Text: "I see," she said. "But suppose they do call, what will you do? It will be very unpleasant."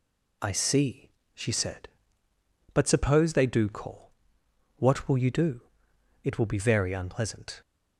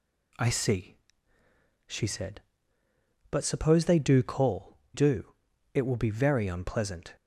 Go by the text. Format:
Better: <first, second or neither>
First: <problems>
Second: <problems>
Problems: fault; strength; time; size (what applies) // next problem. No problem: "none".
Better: first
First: none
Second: skips "what will you"; at 4.8 s